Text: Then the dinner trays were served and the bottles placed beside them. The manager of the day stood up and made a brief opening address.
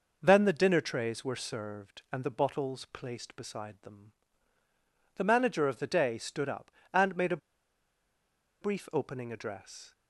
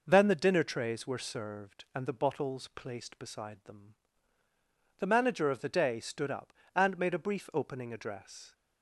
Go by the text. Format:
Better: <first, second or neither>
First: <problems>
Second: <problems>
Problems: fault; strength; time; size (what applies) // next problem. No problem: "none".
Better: second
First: pauses between "a" and "brief"; at 7.3 s; 1.2 s long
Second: none